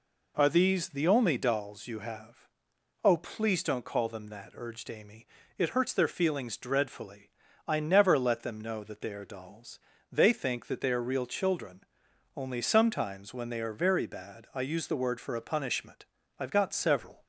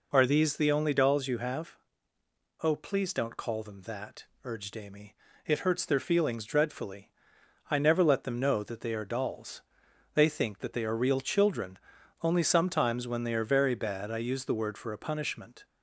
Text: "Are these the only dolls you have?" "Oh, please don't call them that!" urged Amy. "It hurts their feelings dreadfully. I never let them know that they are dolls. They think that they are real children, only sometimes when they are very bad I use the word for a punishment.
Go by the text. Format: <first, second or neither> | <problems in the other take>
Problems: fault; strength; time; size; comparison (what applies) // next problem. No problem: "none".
second | goes on to say "I've got several"; noticeable; from 16.3 s on; 0.84 s long